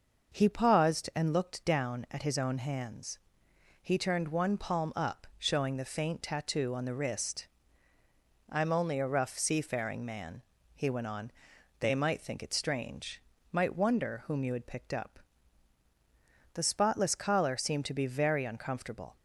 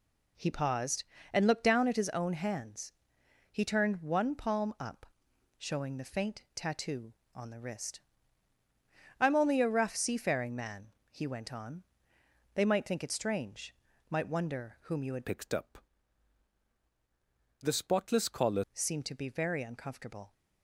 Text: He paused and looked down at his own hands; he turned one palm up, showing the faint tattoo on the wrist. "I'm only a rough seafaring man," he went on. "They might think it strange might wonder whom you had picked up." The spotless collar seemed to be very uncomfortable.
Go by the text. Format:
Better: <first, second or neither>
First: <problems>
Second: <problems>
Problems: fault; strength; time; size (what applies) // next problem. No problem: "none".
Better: first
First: pauses between "strange" and "might"; slight; at 13.2 s; 0.30 s long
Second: pauses between "strange" and "might"; slight; at 13.7 s; 0.36 s long // changes voice from "picked" to "collar"; from 15.2 to 18.6 s; 3.4 s long